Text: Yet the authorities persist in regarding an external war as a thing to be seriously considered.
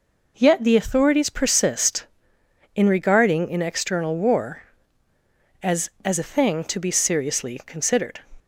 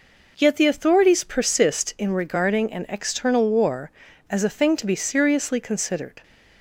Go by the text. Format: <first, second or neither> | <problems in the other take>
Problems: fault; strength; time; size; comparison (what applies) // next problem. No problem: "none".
second | says "as" twice; at 6.0 s